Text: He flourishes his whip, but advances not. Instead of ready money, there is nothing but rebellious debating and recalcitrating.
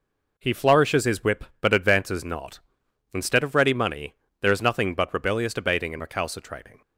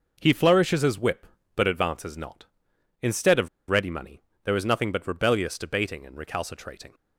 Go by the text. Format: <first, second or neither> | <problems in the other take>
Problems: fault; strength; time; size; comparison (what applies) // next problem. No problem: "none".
first | pauses between "of" and "ready"; slight; at 3.4 s; 0.21 s long